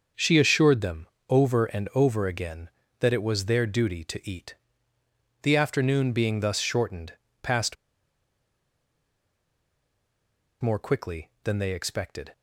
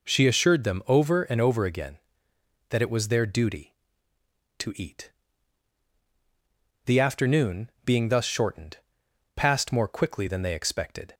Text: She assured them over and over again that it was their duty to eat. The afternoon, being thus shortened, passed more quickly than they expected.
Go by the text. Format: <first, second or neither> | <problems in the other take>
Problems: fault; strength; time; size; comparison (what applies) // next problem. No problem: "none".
second | starts louder than the rest; until 1.3 s; 6.5 dB // pauses between "them" and "over"; slight; at 1.0 s; 0.20 s long // pauses between "passed" and "more"; strong; at 7.7 s; 2.8 s long